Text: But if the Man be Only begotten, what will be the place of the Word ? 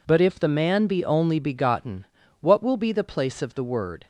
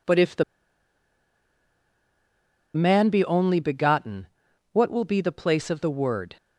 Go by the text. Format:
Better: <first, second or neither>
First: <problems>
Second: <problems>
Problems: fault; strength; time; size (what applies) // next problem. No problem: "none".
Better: first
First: none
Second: pauses between "the" and "Man"; strong; at 0.4 s; 2.3 s long